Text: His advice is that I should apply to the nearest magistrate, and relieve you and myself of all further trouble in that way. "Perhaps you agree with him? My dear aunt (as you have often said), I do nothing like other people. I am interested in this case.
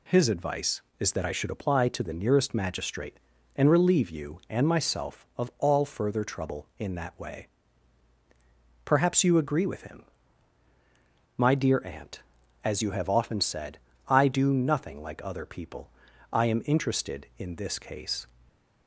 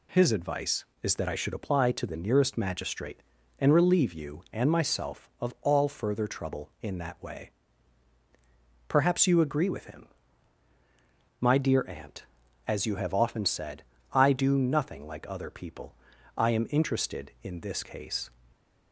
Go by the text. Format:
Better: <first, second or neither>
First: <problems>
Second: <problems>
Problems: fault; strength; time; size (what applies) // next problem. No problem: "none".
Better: neither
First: none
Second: none